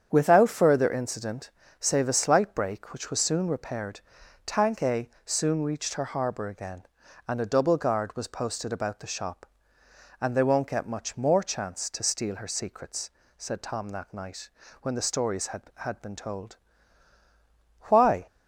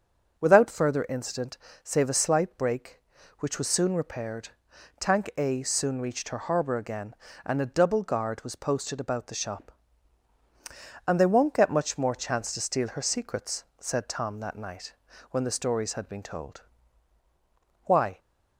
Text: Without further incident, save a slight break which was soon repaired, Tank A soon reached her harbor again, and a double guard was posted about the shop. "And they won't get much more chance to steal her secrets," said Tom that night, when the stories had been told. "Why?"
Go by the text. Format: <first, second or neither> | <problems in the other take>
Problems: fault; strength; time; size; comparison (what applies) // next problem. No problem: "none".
second | starts louder than the rest; strong; until 1.1 s; 8 dB; also in the second // pauses between "A" and "soon"; slight; at 5.0 s; 0.16 s long // says "had" twice; at 15.7 s